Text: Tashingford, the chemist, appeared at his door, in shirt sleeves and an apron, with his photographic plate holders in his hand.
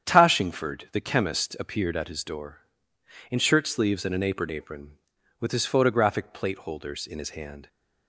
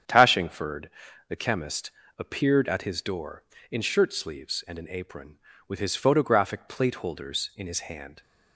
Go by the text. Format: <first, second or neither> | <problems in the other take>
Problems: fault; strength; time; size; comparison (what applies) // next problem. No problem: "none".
second | starts louder than the rest; strong; until 1.1 s; 8.5 dB; strong in the second // says "apron" twice; at 4.4 s